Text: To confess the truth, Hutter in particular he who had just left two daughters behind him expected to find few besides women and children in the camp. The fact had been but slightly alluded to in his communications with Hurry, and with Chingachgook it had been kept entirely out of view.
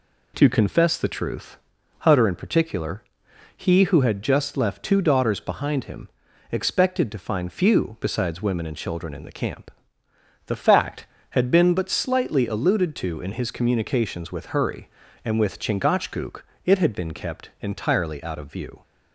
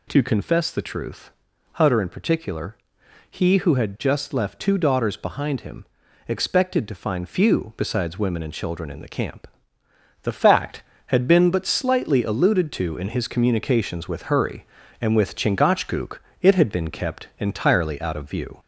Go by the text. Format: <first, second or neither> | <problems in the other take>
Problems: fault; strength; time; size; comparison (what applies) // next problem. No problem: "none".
first | gets louder; slight; throughout; 2 dB // pauses between "particular" and "he"; noticeable; at 2.7 s; 0.52 s long; noticeable in the first // pauses between "him" and "expected"; at 5.8 s; 0.42 s long; also in the first // pauses between "Chingachgook" and "it"; slight; at 16.1 s; 0.22 s long; slight in the first